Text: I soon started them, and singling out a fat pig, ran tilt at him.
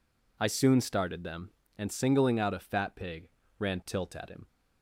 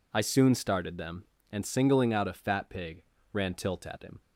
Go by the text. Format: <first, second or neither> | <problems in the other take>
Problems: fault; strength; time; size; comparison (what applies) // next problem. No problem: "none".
neither | none